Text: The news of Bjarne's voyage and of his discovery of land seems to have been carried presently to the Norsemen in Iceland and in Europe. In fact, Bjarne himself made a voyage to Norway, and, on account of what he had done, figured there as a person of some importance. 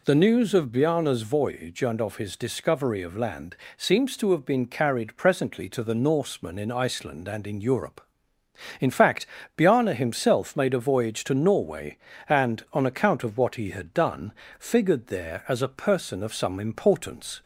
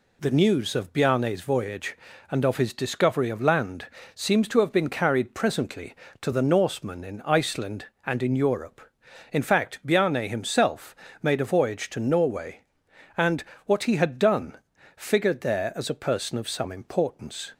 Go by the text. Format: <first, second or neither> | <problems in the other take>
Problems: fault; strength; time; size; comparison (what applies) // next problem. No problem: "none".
first | pauses between "land" and "seems"; slight; at 3.8 s; 0.28 s long; slight in the first // pauses between "himself" and "made"; slight; at 10.9 s; 0.26 s long // skips "on account of"; at 13.5 s